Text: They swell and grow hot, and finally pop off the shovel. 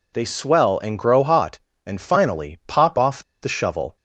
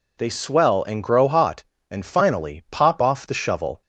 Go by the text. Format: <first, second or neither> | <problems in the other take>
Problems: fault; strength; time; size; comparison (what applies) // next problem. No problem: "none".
second | pauses between "off" and "the"; slight; at 3.2 s; 0.18 s long